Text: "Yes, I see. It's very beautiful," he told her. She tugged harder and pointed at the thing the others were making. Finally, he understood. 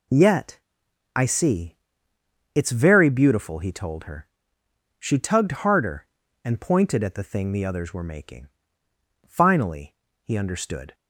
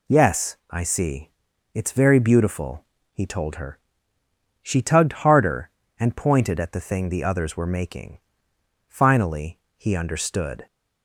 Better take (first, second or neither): second